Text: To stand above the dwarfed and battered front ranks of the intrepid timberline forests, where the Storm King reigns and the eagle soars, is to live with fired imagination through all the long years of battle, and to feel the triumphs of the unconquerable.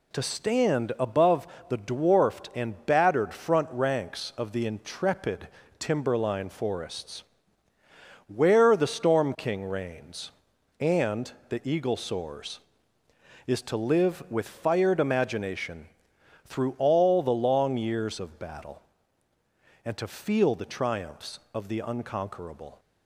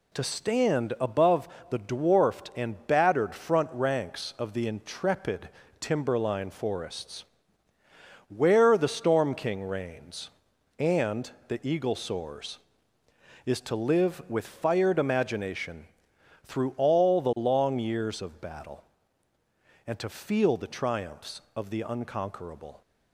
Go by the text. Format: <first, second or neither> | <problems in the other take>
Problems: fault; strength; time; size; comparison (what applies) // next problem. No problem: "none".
neither | pauses between "above" and "the"; slight; the same in both // pauses between "intrepid" and "timberline"; slight; the same in both // pauses between "and" and "the"; slight; the same in both // pauses between "imagination" and "through"; noticeable; the same in both